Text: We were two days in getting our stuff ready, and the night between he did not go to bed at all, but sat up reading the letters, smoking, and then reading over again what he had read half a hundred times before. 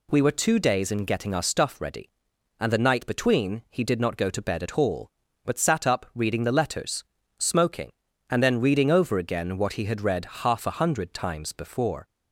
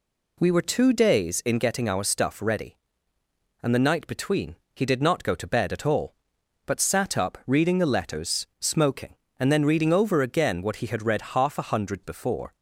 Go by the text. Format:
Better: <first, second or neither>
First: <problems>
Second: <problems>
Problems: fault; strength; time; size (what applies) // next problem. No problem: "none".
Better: first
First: none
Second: pauses between "between" and "he"; slight; at 4.5 s; 0.18 s long // skips "times"; at 12.0 s